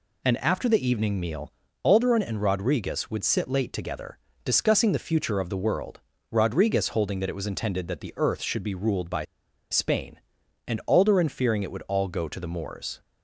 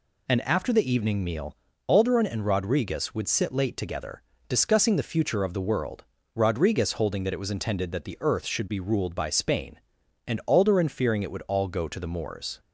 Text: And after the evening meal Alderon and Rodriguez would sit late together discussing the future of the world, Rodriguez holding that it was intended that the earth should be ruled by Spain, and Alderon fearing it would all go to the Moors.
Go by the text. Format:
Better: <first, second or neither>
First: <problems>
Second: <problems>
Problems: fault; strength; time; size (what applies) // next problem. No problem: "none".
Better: second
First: pauses between "meal" and "Alderon"; slight; at 1.5 s; 0.32 s long // pauses between "together" and "discussing"; slight; at 4.1 s; 0.26 s long // pauses between "by" and "Spain"; noticeable; at 9.2 s; 0.46 s long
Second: pauses between "meal" and "Alderon"; slight; at 1.5 s; 0.32 s long // pauses between "together" and "discussing"; slight; at 4.2 s; 0.26 s long